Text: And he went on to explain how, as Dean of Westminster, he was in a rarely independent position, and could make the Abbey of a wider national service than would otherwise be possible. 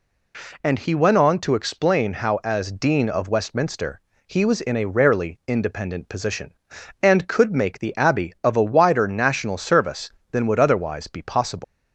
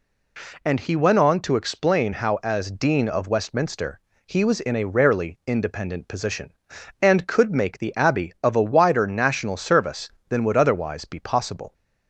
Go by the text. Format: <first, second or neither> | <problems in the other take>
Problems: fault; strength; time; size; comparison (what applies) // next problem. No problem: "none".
second | leaves "possible" unfinished; at 11.6 s; 110 ms